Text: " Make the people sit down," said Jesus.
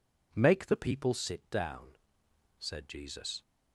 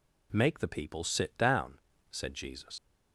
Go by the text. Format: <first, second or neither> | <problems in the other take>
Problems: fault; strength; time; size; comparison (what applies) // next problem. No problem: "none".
first | leaves "Jesus" unfinished; at 2.7 s; 70 ms